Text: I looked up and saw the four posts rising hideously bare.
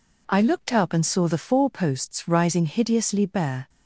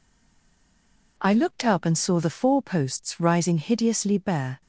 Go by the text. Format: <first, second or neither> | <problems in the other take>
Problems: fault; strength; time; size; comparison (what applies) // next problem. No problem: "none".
first | stays silent before the first word; noticeable; until 1.1 s; 1.1 s long